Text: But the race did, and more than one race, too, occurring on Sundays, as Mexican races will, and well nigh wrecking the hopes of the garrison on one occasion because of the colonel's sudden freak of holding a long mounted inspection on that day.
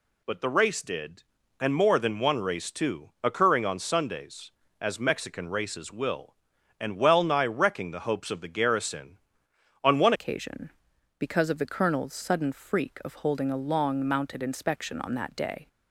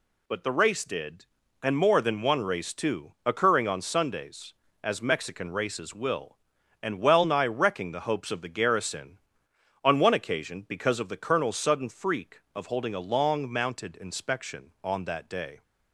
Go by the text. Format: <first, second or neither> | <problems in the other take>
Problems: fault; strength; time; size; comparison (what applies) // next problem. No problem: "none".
second | changes voice at "occasion"; from 10.1 s on; 5.5 s long